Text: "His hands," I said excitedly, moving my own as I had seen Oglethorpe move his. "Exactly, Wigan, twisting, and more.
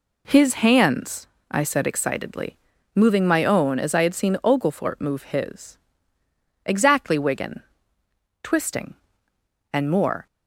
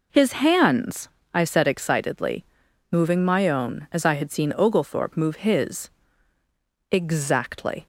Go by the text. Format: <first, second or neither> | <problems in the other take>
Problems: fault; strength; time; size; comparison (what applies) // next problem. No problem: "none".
first | stops before "Wigan twisting and more"; at 7.8 s